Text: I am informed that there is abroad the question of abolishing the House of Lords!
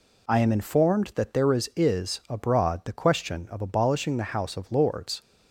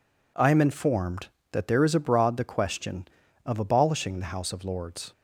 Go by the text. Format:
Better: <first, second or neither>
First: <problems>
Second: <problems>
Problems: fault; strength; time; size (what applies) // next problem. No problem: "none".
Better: second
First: says "is" twice; at 1.7 s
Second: none